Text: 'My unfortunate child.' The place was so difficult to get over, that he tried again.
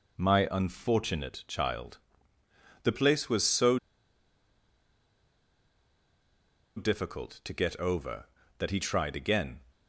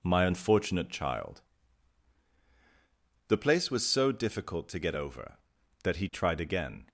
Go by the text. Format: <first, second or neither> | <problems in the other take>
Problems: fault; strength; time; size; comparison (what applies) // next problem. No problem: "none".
second | pauses between "so" and "difficult"; strong; at 3.7 s; 2.9 s long